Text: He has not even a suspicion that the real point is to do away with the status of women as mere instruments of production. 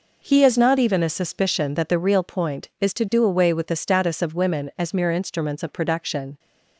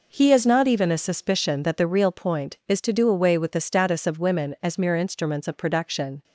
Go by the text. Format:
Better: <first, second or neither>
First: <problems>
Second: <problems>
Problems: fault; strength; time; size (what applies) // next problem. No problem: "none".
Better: neither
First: none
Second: none